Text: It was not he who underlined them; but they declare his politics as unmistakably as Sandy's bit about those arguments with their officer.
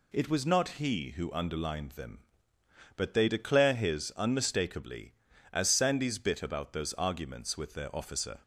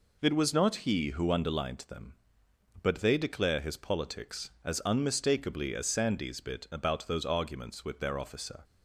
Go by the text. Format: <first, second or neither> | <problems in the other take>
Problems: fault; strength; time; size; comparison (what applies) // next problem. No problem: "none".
second | skips "politics as"; at 4.1 s